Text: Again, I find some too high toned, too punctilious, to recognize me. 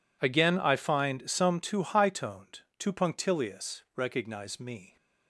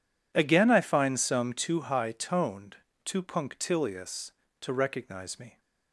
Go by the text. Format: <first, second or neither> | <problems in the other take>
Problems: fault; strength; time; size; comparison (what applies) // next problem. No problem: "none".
second | skips "to"; at 3.8 s